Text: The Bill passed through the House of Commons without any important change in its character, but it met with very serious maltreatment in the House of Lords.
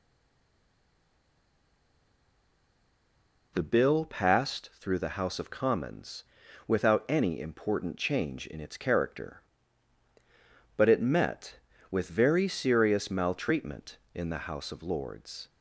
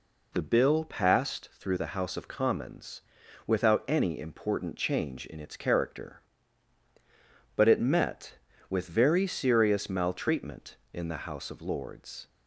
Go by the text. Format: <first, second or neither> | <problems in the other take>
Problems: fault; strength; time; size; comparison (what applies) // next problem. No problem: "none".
second | stays silent before the first word; strong; until 3.5 s; 3.5 s long // pauses between "Commons" and "without"; at 6.2 s; 0.44 s long; noticeable in the second